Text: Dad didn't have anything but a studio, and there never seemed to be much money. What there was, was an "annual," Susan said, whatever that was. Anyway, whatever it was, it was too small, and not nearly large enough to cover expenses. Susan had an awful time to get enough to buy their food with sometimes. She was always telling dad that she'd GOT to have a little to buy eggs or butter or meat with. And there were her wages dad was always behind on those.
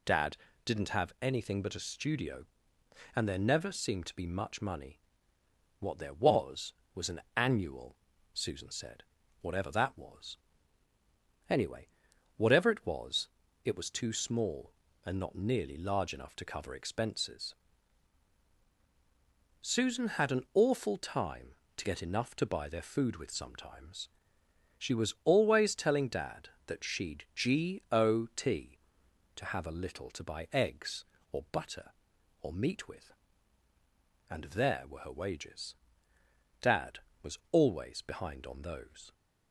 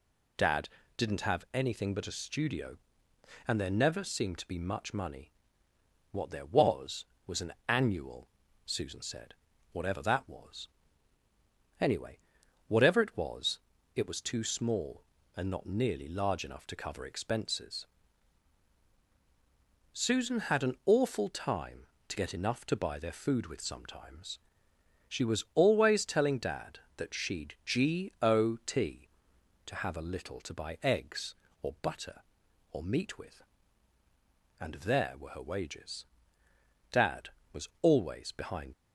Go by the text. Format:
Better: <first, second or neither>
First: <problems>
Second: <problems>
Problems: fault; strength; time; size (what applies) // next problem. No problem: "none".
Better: first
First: pauses between "Dad" and "didn't"; slight; at 0.3 s; 0.30 s long // pauses between "wages" and "dad"; noticeable; at 35.7 s; 0.88 s long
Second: pauses between "Dad" and "didn't"; slight; at 0.6 s; 0.30 s long // pauses between "wages" and "dad"; noticeable; at 36.0 s; 0.88 s long // stops before "on those"; at 38.7 s